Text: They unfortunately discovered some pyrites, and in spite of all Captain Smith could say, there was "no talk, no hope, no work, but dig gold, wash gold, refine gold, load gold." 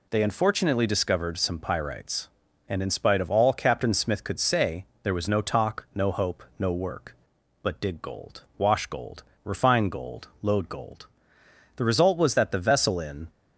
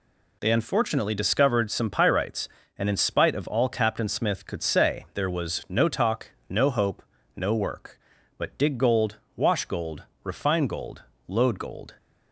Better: second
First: goes on to say "The result was that the vessel in"; from 11.7 s on; 1.5 s long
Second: none

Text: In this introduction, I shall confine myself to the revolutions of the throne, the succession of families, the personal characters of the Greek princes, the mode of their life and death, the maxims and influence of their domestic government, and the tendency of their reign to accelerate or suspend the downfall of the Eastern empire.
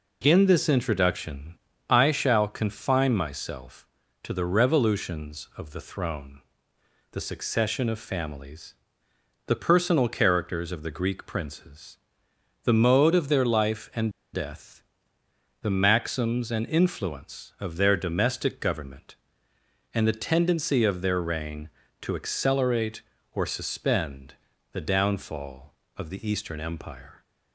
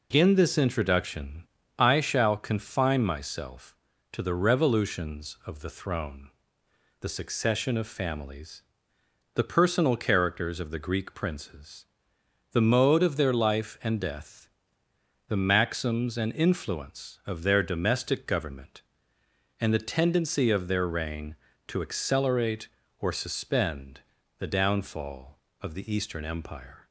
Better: second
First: pauses between "and" and "death"; slight; at 14.1 s; 0.22 s long // pauses between "suspend" and "the"; at 24.3 s; 0.38 s long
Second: pauses between "suspend" and "the"; at 24.0 s; 0.38 s long

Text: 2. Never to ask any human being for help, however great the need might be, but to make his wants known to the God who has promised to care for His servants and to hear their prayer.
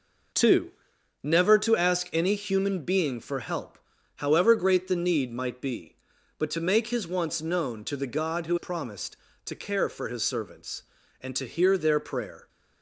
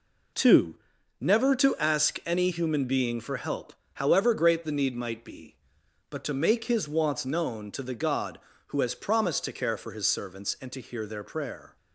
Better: second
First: skips "has"; at 8.5 s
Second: none

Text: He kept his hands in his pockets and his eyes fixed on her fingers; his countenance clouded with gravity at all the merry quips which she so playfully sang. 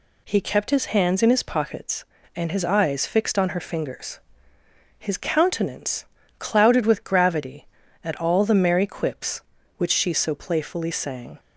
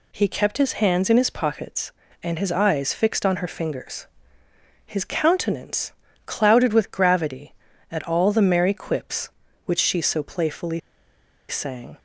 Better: first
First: pauses between "countenance" and "clouded"; slight; at 6.0 s; 0.32 s long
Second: pauses between "countenance" and "clouded"; slight; at 5.9 s; 0.32 s long // pauses between "playfully" and "sang"; noticeable; at 10.8 s; 0.69 s long

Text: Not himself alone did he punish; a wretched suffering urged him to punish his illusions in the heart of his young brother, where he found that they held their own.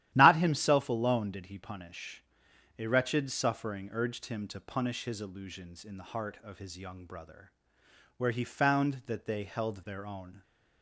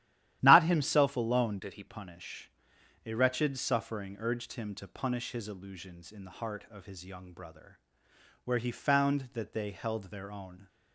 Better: first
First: starts louder than the rest; strong; until 1.1 s; 12.5 dB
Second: starts louder than the rest; strong; until 1.4 s; 12.5 dB // changes voice from "did" to "he"; from 1.6 to 1.8 s; 0.2 s long

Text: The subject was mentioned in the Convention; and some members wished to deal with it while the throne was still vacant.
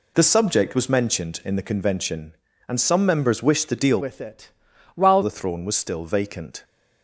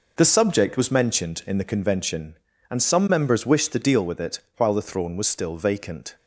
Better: second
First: changes voice from "with" to "while"; from 4.0 to 5.2 s; 1.2 s long // pauses between "it" and "while"; at 4.5 s; 0.44 s long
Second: pauses between "it" and "while"; slight; at 4.3 s; 0.18 s long

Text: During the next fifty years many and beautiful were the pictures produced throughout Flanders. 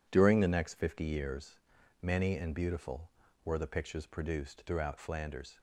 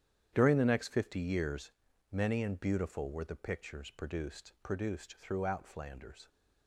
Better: first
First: pauses between "years" and "many"; at 1.5 s; 0.44 s long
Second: starts louder than the rest; strong; until 1.3 s; 9.5 dB // pauses between "years" and "many"; at 1.6 s; 0.40 s long // says "produced" twice; at 4.6 s

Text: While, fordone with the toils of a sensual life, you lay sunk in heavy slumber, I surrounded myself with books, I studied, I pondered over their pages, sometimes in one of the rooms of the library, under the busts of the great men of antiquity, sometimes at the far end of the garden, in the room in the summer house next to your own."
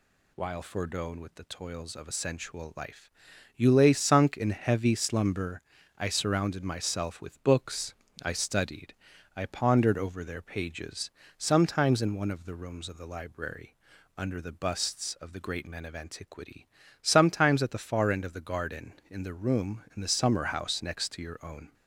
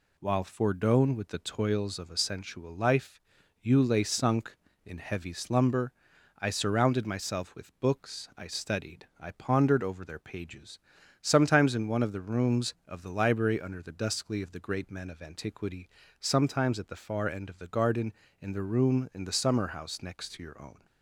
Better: first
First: none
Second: says "duskly" for "busts"; at 13.9 s

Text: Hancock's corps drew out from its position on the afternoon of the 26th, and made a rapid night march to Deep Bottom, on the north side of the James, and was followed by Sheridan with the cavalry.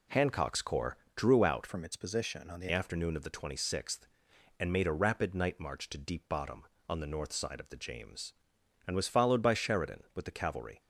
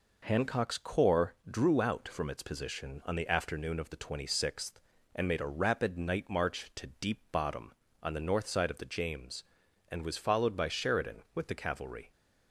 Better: second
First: pauses between "corps" and "drew"; slight; at 0.9 s; 0.18 s long // changes voice from "from" to "the"; from 1.6 to 2.6 s; 1.0 s long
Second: pauses between "corps" and "drew"; slight; at 1.3 s; 0.18 s long

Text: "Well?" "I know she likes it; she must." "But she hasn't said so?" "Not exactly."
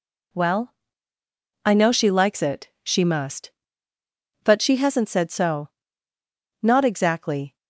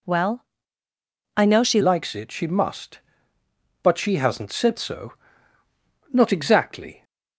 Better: first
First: none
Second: changes voice at "likes"; from 1.8 s on; 5.2 s long

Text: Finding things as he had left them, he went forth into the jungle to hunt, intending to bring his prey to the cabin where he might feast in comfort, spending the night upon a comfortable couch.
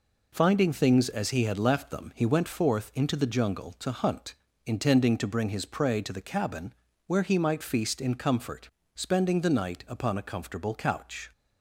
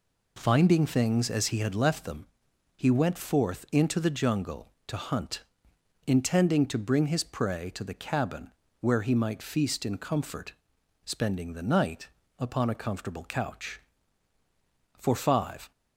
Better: first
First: pauses between "cabin" and "where"; slight; at 6.7 s; 0.32 s long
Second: pauses between "cabin" and "where"; slight; at 8.5 s; 0.28 s long // pauses between "night" and "upon"; slight; at 12.0 s; 0.28 s long // goes on to say "For five"; noticeable; from 14.9 s on; 0.72 s long

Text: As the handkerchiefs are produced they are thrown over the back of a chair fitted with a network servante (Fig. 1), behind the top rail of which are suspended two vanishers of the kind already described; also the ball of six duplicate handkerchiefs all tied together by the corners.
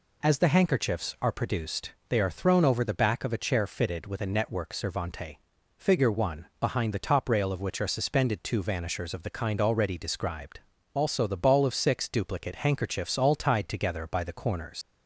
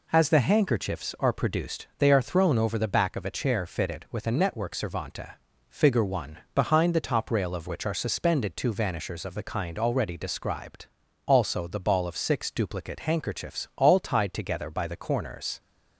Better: second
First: pauses between "produced" and "they"; slight; at 1.9 s; 0.18 s long // leaves "corners" unfinished; at 14.8 s; 105 ms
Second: none

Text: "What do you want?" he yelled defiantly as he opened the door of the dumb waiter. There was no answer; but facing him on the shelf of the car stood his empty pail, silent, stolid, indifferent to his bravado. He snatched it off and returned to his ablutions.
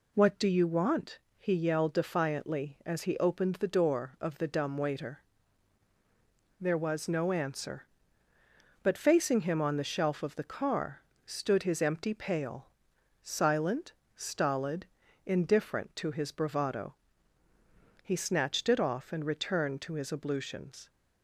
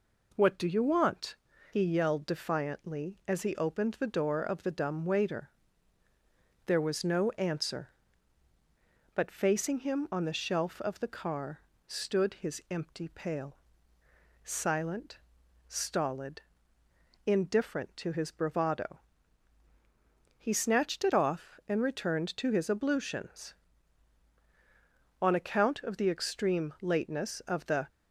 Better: first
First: pauses between "car" and "stood"; slight; at 11.0 s; 0.26 s long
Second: pauses between "car" and "stood"; slight; at 11.6 s; 0.26 s long // goes on to say "On account of the extreme lateness of the"; strong; from 25.2 s on; 2.6 s long

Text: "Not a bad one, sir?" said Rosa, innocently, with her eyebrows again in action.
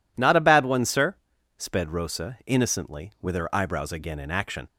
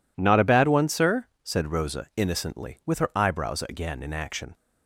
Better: second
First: says "sped" for "said"; at 1.5 s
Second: none

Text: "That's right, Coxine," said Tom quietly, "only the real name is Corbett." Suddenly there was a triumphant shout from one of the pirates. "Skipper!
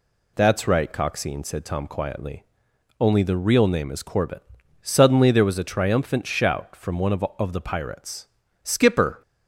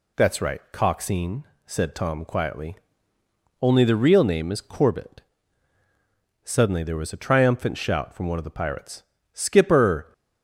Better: second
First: says "of" twice; at 7.3 s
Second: none

